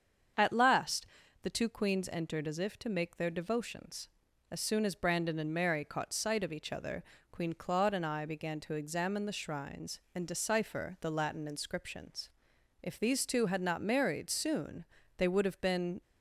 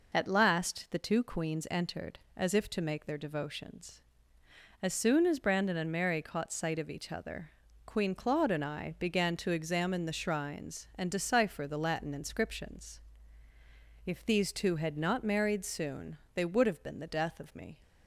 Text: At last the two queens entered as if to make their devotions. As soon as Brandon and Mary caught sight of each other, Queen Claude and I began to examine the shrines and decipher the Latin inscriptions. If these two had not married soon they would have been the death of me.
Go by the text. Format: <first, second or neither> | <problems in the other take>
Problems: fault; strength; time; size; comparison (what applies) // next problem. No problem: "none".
second | starts louder than the rest; strong; until 1.7 s; 7 dB // pauses between "last" and "the"; slight; at 1.0 s; 0.36 s long // pauses between "soon" and "they"; slight; at 14.8 s; 0.34 s long; slight in the second // stops before "the death of me"; at 16.0 s